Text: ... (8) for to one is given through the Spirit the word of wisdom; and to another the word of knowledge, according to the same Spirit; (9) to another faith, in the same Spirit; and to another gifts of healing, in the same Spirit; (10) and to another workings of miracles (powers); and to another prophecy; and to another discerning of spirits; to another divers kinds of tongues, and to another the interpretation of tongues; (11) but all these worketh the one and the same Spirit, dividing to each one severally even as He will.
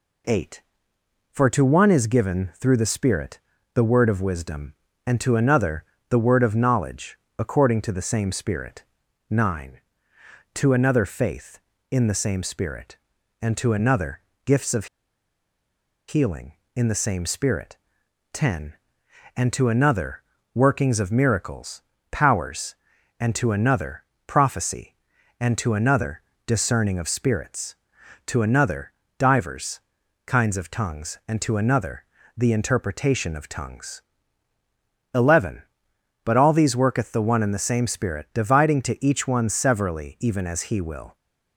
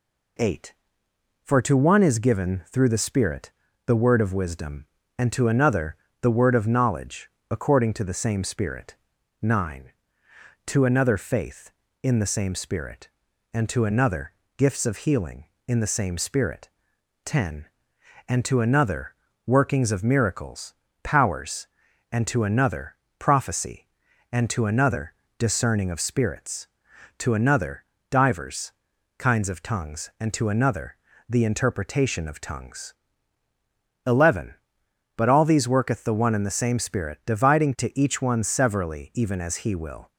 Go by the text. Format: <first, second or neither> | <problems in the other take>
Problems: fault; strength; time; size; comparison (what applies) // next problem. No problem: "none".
second | pauses between "Spirit" and "the"; slight; at 3.3 s; 0.36 s long; slight in the second // pauses between "another" and "the"; slight; at 5.8 s; 0.26 s long; slight in the second // pauses between "another" and "gifts"; slight; at 14.2 s; 0.24 s long; slight in the second // pauses between "of" and "healing"; at 14.8 s; 1.2 s long // pauses between "another" and "workings"; slight; at 20.2 s; 0.32 s long; slight in the second // pauses between "another" and "prophecy"; slight; at 24.0 s; 0.24 s long; slight in the second // pauses between "another" and "discerning"; slight; at 26.2 s; 0.24 s long; slight in the second // pauses between "another" and "divers"; slight; at 28.9 s; 0.28 s long; slight in the second // pauses between "divers" and "kinds"; noticeable; at 29.7 s; 0.46 s long; noticeable in the second // pauses between "another" and "the"; slight; at 32.0 s; 0.32 s long; slight in the second